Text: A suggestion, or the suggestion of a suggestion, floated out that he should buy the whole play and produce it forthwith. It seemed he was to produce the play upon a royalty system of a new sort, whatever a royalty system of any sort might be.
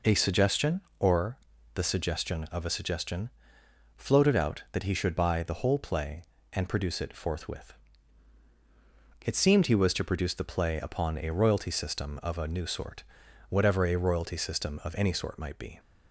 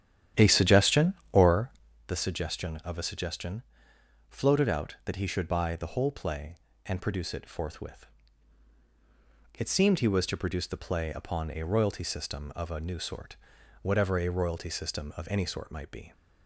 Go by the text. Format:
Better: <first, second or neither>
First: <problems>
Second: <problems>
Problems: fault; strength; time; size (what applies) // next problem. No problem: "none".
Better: first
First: pauses between "or" and "the"; at 1.3 s; 0.38 s long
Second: starts louder than the rest; strong; until 2.0 s; 10.5 dB // pauses between "or" and "the"; at 1.7 s; 0.38 s long